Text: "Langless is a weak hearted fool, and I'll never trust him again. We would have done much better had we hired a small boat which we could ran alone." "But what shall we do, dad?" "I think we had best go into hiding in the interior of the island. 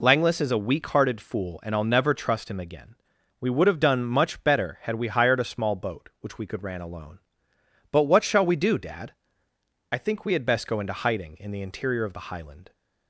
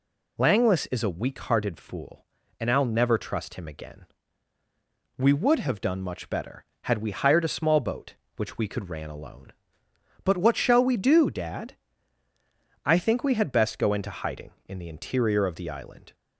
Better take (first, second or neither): second